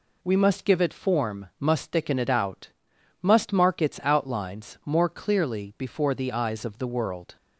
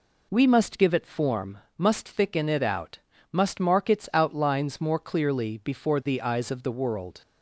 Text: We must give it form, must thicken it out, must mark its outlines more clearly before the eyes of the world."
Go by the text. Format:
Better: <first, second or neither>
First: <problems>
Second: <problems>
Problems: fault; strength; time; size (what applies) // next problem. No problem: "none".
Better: neither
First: none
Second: none